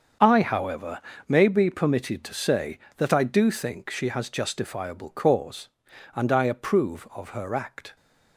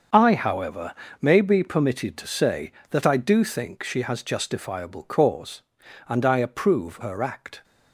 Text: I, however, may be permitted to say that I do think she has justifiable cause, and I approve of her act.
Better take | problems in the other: first | starts louder than the rest; until 1.3 s; 7 dB; also in the first // skips "of"; at 6.9 s

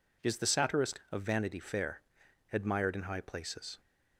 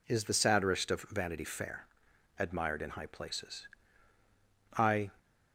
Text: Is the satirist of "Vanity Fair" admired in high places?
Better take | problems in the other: first | pauses between "Fair" and "admired"; noticeable; at 1.8 s; 0.52 s long; noticeable in the first // goes on to say "I"; slight; from 4.7 s on; 0.38 s long

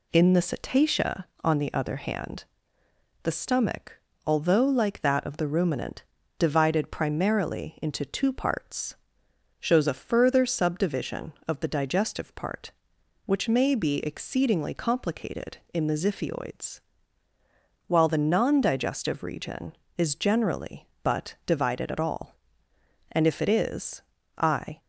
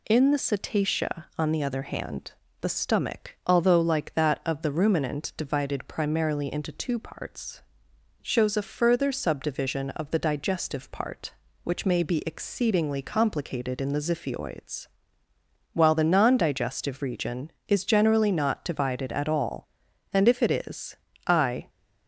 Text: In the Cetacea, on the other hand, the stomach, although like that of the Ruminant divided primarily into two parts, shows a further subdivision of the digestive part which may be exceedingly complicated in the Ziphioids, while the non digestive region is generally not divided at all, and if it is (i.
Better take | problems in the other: second | pauses between "Ruminant" and "divided"; slight; at 6.0 s; 0.36 s long // says "but" for "not"; at 21.0 s

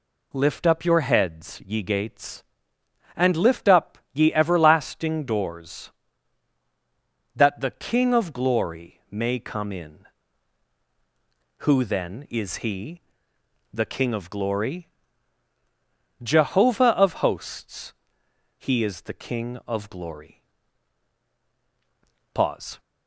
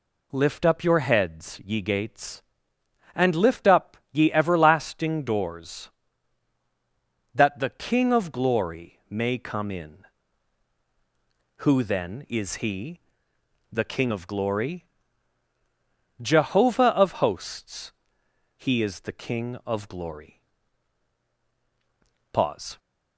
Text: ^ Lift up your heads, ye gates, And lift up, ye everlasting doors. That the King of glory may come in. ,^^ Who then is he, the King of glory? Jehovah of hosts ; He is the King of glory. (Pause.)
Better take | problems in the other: neither | none

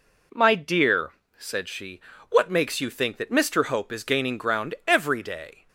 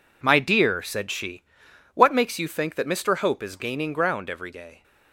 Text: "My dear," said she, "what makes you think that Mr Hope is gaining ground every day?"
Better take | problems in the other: neither | none

